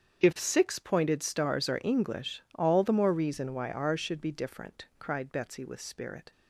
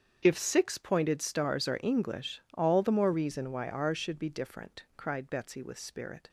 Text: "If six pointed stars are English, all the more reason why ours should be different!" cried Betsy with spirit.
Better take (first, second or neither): neither